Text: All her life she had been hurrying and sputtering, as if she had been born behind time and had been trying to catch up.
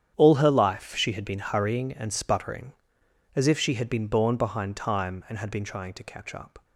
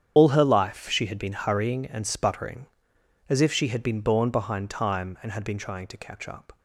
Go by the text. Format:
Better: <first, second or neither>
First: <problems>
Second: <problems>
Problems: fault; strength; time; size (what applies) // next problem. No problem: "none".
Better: first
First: starts louder than the rest; strong; until 1.1 s; 9 dB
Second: loses the start of "All"; at 0.1 s; 60 ms // starts louder than the rest; strong; until 1.1 s; 9 dB